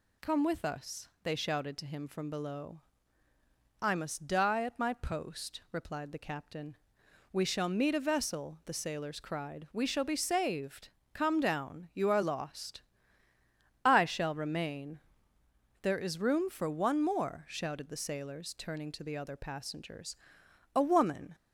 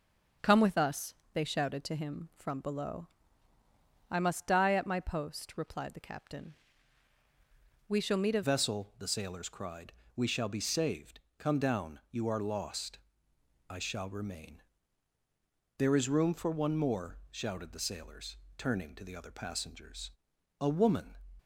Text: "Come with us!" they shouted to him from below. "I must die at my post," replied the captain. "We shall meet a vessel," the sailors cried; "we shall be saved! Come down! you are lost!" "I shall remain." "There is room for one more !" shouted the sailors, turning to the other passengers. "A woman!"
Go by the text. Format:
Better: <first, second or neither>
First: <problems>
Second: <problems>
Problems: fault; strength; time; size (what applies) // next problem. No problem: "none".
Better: first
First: none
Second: starts louder than the rest; until 1.6 s; 6.5 dB // changes voice at "vessel"; from 8.4 s on; 12.7 s long